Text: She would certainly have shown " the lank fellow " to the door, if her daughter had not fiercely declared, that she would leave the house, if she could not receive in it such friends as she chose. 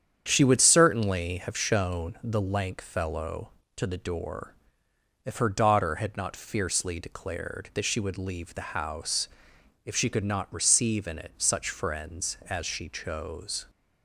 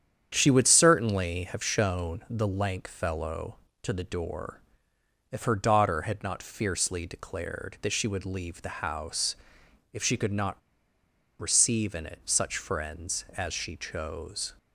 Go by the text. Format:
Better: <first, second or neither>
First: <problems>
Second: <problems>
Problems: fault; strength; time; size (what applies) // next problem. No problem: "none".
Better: first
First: starts louder than the rest; strong; until 1.2 s; 8.5 dB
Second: starts louder than the rest; strong; until 1.3 s; 9 dB // pauses between "not" and "receive"; noticeable; at 10.5 s; 0.80 s long